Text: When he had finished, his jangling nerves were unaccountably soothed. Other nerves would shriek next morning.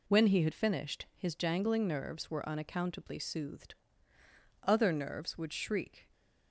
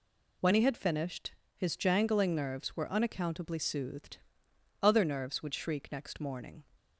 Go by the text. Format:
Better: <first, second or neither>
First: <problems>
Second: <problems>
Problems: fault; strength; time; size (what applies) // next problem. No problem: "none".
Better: second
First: stops before "next morning"; at 6.1 s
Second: none